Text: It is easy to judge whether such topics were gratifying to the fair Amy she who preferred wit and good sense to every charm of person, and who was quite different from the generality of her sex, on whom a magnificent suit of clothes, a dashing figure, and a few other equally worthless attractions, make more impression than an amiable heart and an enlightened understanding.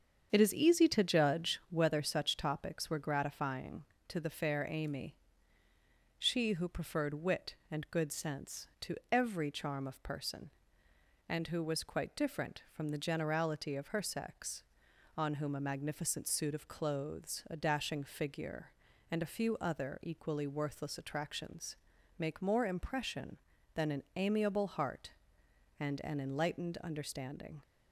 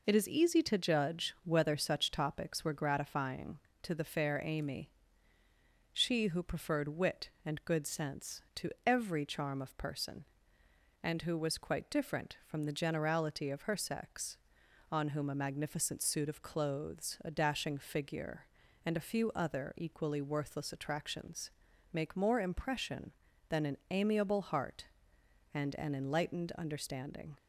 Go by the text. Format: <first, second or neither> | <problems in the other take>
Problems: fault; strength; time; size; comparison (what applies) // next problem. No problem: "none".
second | starts louder than the rest; strong; until 1.7 s; 7.5 dB // pauses between "Amy" and "she"; at 5.1 s; 1.0 s long; also in the second // pauses between "to" and "every"; slight; at 8.9 s; 0.16 s long; slight in the second